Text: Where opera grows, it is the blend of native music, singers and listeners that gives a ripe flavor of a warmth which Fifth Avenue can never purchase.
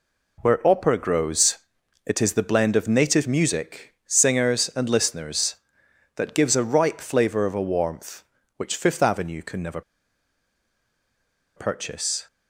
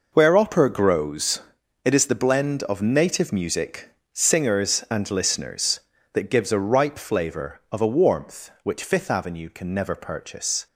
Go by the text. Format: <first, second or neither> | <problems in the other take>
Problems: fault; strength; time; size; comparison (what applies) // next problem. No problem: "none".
second | pauses between "never" and "purchase"; strong; at 9.8 s; 1.7 s long